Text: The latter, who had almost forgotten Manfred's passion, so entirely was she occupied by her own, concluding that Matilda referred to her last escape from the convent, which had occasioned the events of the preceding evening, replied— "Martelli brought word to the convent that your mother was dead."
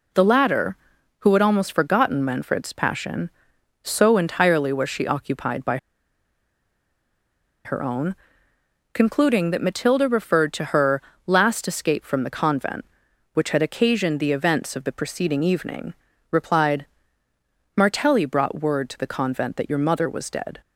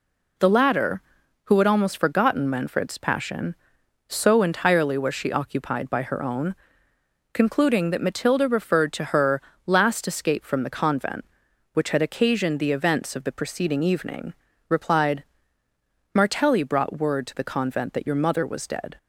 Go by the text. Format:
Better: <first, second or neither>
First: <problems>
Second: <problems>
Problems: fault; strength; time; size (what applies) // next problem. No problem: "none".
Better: second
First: pauses between "by" and "her"; strong; at 5.7 s; 1.8 s long // pauses between "her" and "last"; slight; at 11.0 s; 0.24 s long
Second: pauses between "her" and "last"; slight; at 9.4 s; 0.24 s long